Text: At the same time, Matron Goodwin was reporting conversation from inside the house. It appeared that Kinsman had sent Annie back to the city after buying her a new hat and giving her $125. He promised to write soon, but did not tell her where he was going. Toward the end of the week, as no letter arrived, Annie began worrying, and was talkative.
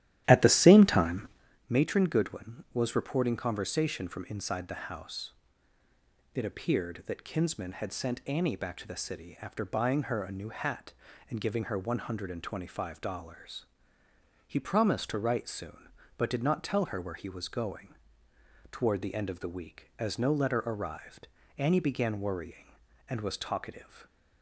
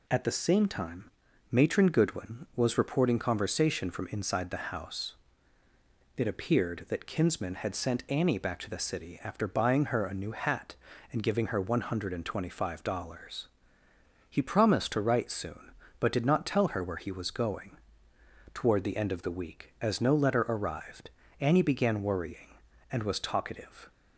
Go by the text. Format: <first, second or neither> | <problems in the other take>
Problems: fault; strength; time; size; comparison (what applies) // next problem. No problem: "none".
second | starts louder than the rest; strong; until 1.6 s; 13 dB